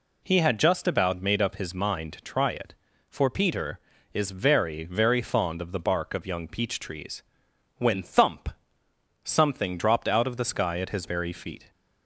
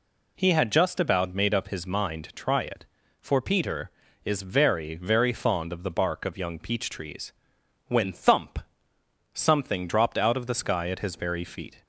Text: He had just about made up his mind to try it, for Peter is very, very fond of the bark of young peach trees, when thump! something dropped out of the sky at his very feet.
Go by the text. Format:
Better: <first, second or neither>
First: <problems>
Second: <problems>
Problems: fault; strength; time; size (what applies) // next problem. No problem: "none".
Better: neither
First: none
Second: none